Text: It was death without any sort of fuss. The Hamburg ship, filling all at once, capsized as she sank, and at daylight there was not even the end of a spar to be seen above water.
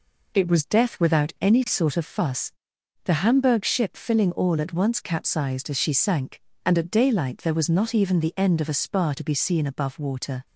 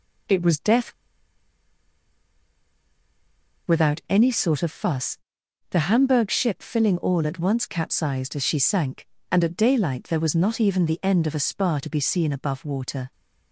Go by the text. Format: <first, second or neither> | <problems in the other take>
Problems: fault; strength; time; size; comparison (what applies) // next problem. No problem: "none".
first | pauses between "death" and "without"; strong; at 0.9 s; 2.7 s long